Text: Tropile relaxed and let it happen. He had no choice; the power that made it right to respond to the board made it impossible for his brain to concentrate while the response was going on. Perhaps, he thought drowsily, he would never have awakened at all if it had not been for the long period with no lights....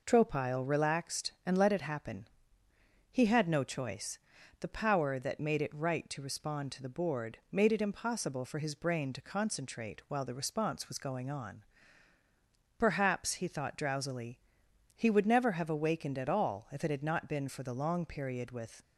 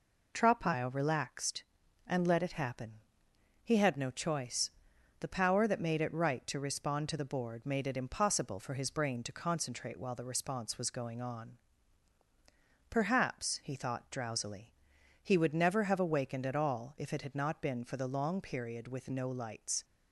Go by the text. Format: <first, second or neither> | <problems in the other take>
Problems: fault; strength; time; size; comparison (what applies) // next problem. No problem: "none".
second | stops before "no lights"; at 18.8 s